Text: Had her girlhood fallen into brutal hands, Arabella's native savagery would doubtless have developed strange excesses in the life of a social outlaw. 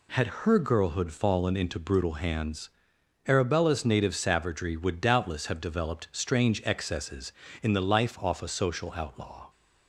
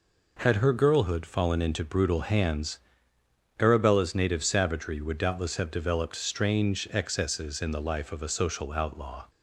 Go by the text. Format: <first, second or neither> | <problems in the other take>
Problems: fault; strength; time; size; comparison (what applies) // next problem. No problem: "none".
second | pauses between "Had" and "her"; slight; at 0.2 s; 0.16 s long // says "off" for "of"; at 8.1 s